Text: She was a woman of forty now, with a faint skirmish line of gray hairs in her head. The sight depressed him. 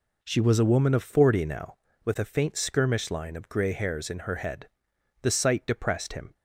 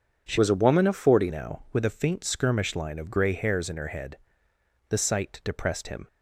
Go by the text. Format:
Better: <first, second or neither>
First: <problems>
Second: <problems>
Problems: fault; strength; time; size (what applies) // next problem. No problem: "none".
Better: first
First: none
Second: changes voice from "was" to "forty"; from 0.3 to 1.3 s; 1.0 s long